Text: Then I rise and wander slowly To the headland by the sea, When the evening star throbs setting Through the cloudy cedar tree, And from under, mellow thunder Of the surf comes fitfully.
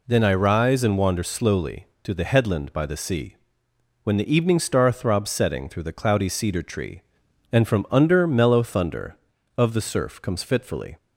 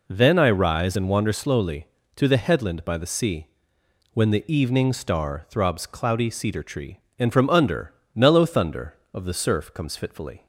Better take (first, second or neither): first